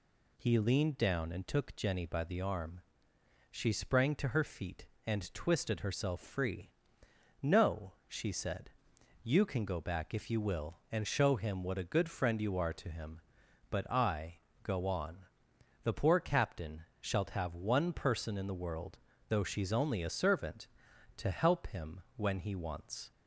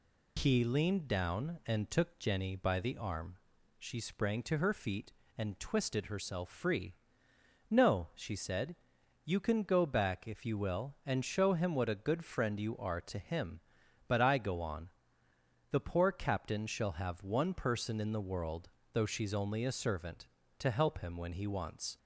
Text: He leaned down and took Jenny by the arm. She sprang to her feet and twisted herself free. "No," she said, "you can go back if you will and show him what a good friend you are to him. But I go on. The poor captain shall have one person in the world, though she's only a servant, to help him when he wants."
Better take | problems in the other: second | pauses between "I" and "go"; slight; at 14.3 s; 0.26 s long // says "shalt" for "shall"; at 17.0 s

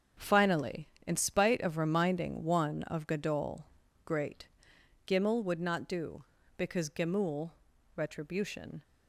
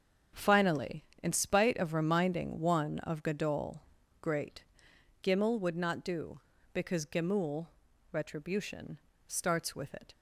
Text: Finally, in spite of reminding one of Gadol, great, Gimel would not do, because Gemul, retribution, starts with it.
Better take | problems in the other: second | starts louder than the rest; until 1.3 s; 7 dB; also in the second // stops before "starts with it"; at 8.8 s

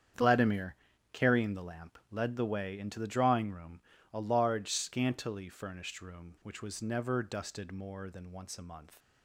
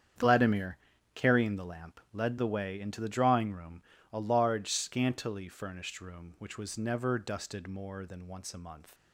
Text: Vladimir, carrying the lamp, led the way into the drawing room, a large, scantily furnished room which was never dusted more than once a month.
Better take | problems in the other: neither | starts louder than the rest; strong; the same in both

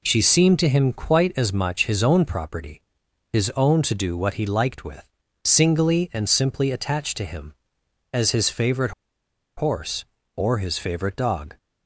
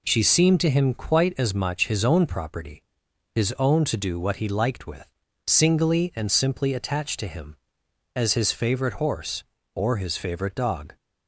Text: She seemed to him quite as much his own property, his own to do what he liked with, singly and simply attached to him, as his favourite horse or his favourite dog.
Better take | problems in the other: second | pauses between "favourite" and "horse"; noticeable; at 8.9 s; 0.65 s long

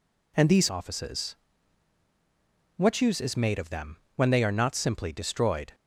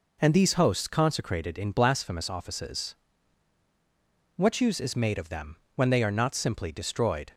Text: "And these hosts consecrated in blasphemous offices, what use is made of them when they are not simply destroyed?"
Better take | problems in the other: second | skips "hosts consecrated in blasphemous"; at 0.6 s // pauses between "them" and "when"; slight; at 3.9 s; 0.20 s long; slight in the second

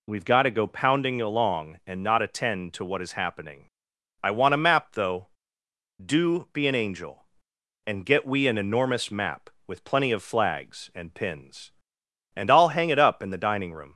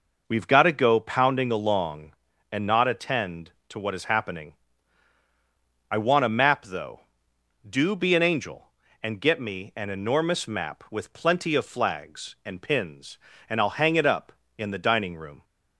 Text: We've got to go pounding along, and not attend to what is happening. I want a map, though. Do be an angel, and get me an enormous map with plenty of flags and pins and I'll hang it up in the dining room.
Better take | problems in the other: second | says "we" for "me"; at 8.2 s

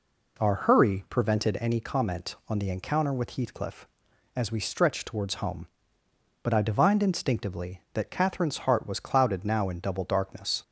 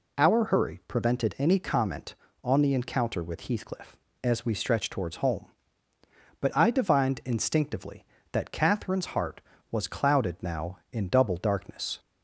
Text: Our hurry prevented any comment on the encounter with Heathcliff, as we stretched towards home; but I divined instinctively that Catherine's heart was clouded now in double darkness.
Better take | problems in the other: neither | none

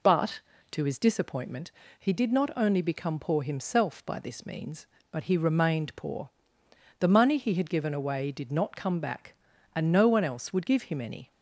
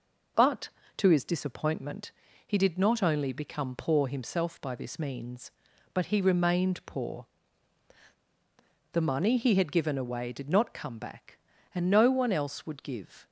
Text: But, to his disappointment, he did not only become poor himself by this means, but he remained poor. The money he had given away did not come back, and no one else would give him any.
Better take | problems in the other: first | stops before "him any"; at 13.2 s

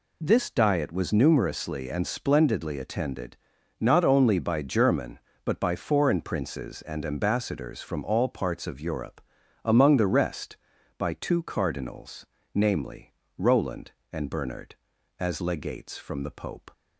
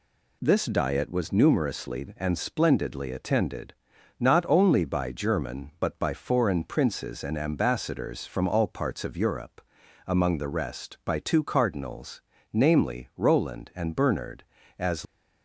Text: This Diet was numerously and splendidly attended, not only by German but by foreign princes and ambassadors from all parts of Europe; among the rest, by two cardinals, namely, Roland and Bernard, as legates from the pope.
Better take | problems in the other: first | stops before "legates from the pope"; at 15.0 s

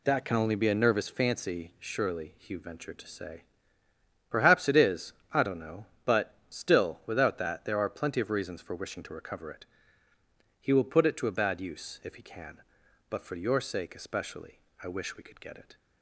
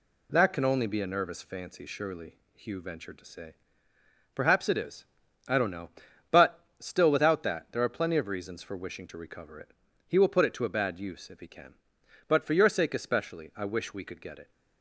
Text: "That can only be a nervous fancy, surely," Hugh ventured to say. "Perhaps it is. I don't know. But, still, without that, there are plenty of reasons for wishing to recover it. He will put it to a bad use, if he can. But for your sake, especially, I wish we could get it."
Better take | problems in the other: neither | none

